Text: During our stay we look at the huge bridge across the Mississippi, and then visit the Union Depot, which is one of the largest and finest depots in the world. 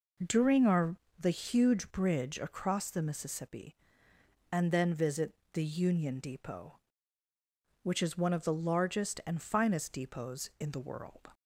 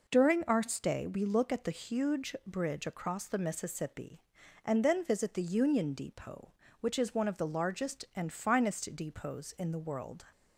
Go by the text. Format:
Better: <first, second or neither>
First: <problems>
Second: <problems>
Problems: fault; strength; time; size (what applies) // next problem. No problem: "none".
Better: second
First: skips "stay we look at"; at 1.0 s // pauses between "visit" and "the"; slight; at 5.3 s; 0.20 s long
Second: none